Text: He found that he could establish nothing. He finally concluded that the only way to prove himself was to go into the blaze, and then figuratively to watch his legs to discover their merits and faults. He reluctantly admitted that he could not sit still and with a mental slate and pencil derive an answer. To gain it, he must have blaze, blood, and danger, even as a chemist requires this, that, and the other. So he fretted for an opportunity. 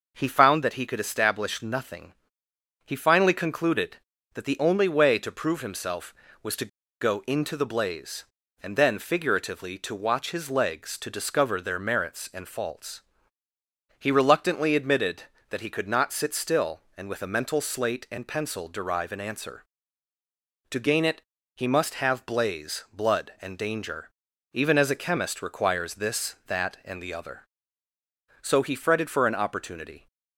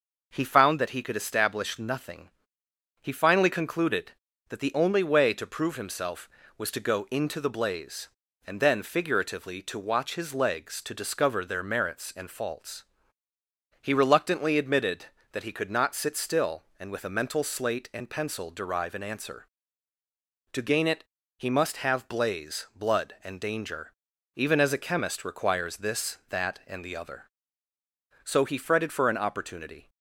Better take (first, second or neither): second